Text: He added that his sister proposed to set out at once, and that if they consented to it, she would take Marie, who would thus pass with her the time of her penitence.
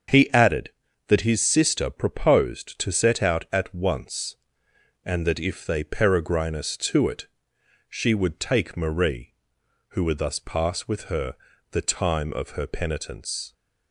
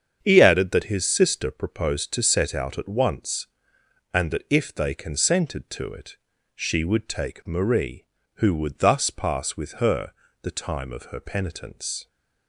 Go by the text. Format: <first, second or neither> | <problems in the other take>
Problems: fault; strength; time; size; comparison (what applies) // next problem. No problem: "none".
second | starts louder than the rest; until 1.4 s; 7 dB; strong in the second // says "peregrinus" for "consented"; at 5.8 s // pauses between "her" and "the"; slight; at 11.3 s; 0.36 s long; slight in the second